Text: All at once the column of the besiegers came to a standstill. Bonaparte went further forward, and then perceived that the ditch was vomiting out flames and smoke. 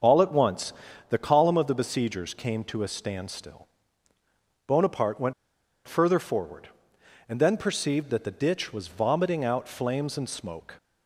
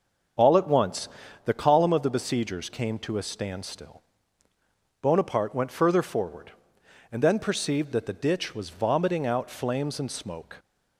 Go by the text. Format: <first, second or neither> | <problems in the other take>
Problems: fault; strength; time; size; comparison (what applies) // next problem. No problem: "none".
second | starts louder than the rest; until 1.3 s; 7 dB; also in the second // pauses between "once" and "the"; slight; at 0.7 s; 0.36 s long; slight in the second // pauses between "went" and "further"; noticeable; at 5.3 s; 0.54 s long